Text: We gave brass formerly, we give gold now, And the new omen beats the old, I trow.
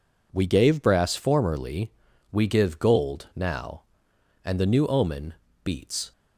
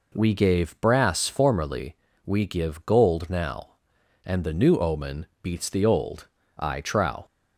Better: second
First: pauses between "omen" and "beats"; slight; at 5.3 s; 0.32 s long // stops before "the old I trow"; at 6.1 s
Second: pauses between "omen" and "beats"; slight; at 5.2 s; 0.16 s long

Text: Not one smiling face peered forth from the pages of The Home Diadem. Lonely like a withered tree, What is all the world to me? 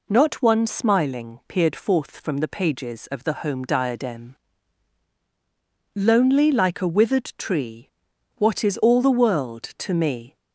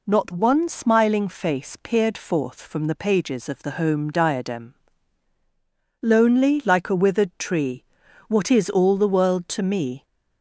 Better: second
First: skips "face"; at 1.4 s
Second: none

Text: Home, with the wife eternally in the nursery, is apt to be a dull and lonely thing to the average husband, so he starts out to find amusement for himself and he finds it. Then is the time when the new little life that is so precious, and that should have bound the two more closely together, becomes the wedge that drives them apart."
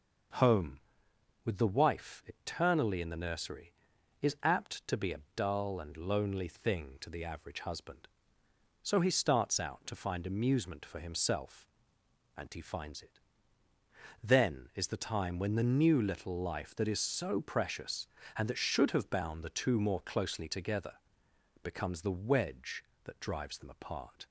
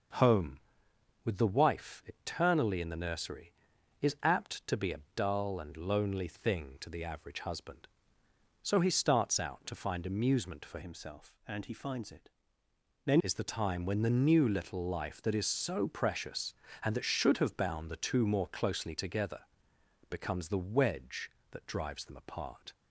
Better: first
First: starts louder than the rest; noticeable; until 2.0 s; 6 dB // pauses between "a" and "dull"; slight; at 5.1 s; 0.16 s long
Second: starts louder than the rest; noticeable; until 1.8 s; 6 dB // pauses between "a" and "dull"; slight; at 4.9 s; 0.16 s long // changes voice from "himself" to "Then"; from 10.8 to 13.2 s; 2.4 s long

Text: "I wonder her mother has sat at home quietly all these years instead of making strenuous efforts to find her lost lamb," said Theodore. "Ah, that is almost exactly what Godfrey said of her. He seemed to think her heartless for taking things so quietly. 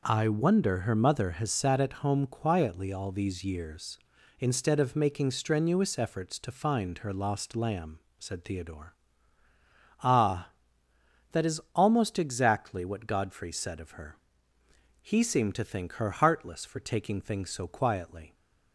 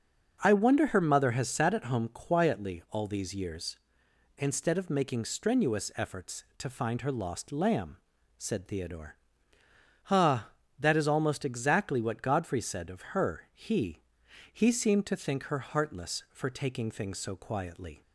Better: first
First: none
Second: starts louder than the rest; until 1.4 s; 7 dB // says "He" twice; at 14.5 s

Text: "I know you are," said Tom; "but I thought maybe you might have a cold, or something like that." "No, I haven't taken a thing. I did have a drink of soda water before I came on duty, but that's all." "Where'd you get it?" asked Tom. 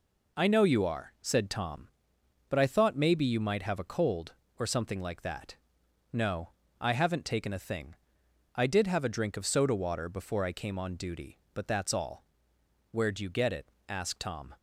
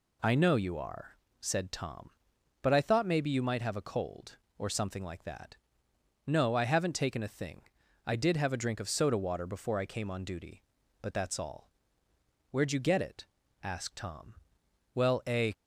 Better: first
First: none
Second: goes on to say "Well a"; from 14.9 s on; 0.60 s long

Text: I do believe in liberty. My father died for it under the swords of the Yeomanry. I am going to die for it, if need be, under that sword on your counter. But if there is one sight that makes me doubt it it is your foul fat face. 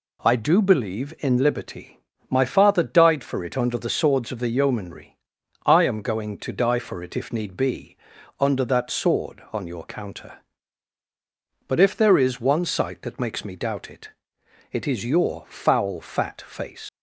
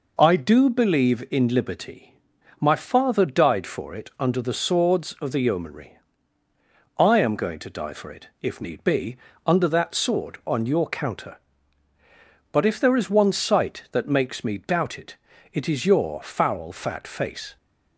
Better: second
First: pauses between "it" and "it"; noticeable; at 14.1 s; 0.62 s long // leaves "face" unfinished; at 16.8 s; 115 ms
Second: pauses between "it" and "it"; slight; at 15.1 s; 0.36 s long

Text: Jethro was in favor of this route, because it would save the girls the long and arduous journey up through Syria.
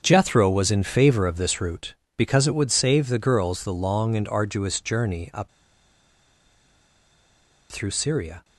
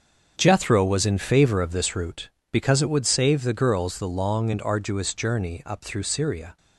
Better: second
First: starts louder than the rest; until 1.0 s; 7 dB // pauses between "up" and "through"; strong; at 5.4 s; 2.2 s long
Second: starts louder than the rest; until 1.3 s; 7 dB

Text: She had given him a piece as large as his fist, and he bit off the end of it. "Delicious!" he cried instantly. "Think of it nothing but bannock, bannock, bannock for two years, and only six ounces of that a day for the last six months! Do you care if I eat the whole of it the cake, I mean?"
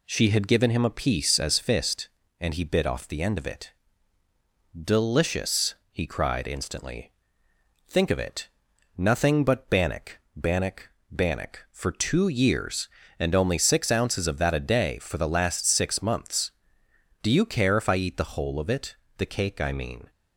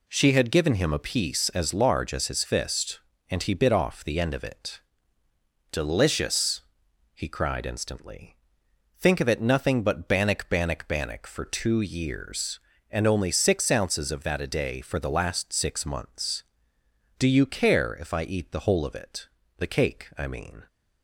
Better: second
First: skips "large as his"; at 1.5 s // pauses between "it" and "nothing"; noticeable; at 8.4 s; 0.50 s long // pauses between "it" and "the"; slight; at 18.9 s; 0.22 s long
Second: pauses between "it" and "the"; slight; at 19.2 s; 0.32 s long

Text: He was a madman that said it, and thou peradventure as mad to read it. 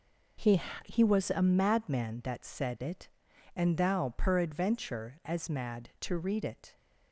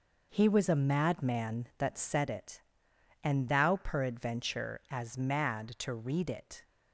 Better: second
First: says "He" twice; at 0.8 s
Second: none

